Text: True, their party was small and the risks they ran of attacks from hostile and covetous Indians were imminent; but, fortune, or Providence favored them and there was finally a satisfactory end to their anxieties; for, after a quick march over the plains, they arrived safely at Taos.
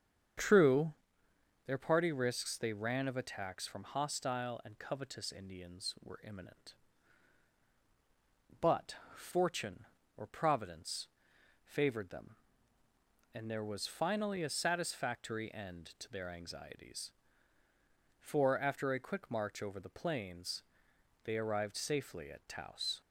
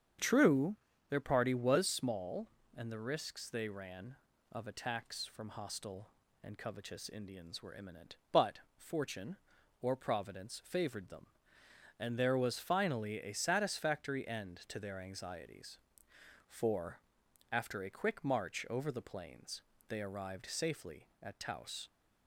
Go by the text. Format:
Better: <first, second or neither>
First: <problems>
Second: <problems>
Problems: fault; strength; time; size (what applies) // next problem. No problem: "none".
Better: second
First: starts louder than the rest; strong; until 2.1 s; 7.5 dB // skips "was small and the"; at 2.1 s // pauses between "Providence" and "favored"; noticeable; at 11.0 s; 0.56 s long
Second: starts louder than the rest; strong; until 1.5 s; 7.5 dB